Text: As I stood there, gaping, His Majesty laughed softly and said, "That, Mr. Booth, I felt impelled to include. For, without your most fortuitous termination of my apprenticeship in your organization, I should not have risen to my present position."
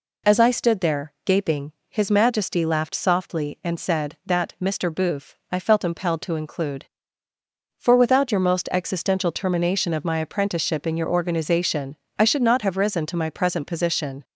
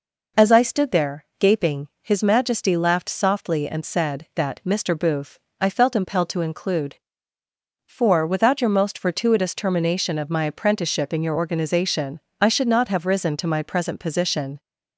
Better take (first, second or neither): second